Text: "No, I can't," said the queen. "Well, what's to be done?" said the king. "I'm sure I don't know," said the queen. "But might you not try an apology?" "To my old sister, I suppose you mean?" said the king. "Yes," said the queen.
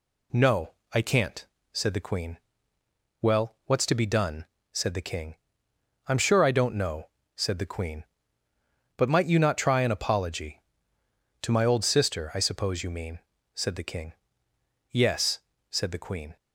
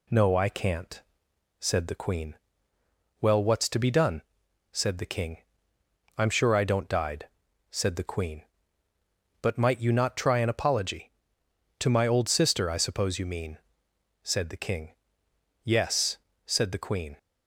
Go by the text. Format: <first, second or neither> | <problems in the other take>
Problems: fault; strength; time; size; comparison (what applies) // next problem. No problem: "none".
first | says "died" for "know"; at 6.8 s